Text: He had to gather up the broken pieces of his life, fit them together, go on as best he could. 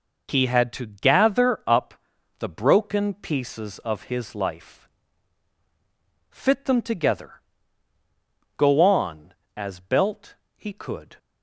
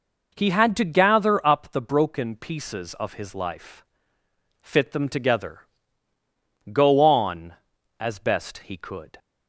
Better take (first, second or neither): second